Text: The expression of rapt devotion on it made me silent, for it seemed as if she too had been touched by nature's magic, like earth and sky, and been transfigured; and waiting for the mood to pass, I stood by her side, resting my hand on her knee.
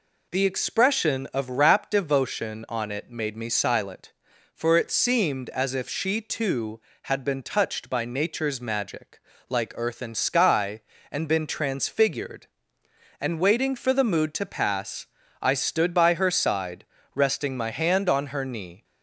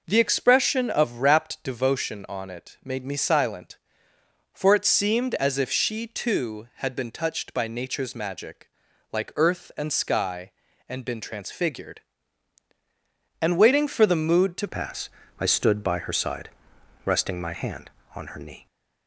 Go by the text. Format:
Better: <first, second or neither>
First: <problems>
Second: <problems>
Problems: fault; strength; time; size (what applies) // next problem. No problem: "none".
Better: first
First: none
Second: changes voice at "pass"; from 14.6 s on; 4.0 s long